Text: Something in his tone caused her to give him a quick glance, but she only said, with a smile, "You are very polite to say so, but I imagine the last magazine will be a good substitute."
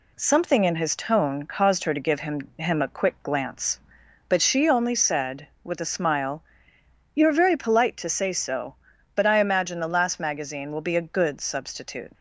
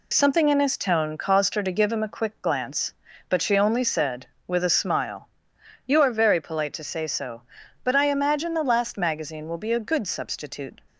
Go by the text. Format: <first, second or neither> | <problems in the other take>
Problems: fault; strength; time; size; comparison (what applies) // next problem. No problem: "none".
second | says "him" twice; at 2.5 s